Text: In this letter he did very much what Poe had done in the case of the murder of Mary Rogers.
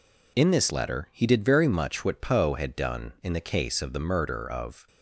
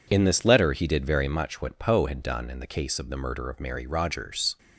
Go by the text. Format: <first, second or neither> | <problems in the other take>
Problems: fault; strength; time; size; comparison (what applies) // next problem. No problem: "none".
second | stops before "Mary Rogers"; at 4.8 s